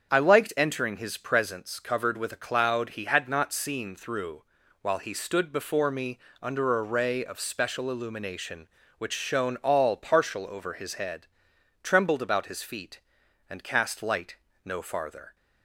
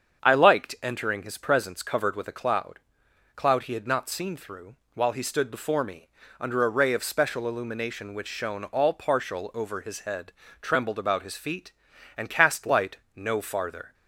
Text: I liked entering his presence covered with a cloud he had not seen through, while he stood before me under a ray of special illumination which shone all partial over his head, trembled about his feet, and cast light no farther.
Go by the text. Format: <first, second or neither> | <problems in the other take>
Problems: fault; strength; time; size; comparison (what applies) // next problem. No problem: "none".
first | starts louder than the rest; strong; until 1.2 s; 7.5 dB; strong in the first // says "cloud" twice; at 3.3 s // pauses between "me" and "under"; slight; at 6.0 s; 0.32 s long; slight in the first // pauses between "light" and "no"; slight; at 12.9 s; 0.18 s long; slight in the first